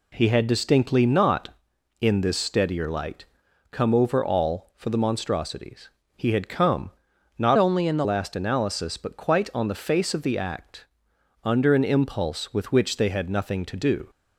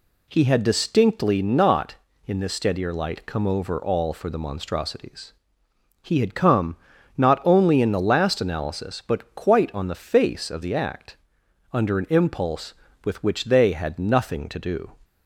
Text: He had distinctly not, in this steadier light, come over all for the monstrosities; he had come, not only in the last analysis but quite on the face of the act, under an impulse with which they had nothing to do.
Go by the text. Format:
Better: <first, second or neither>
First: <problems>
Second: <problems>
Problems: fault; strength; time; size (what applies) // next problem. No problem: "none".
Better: second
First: changes voice from "only" to "the"; from 7.5 to 8.0 s; 0.5 s long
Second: none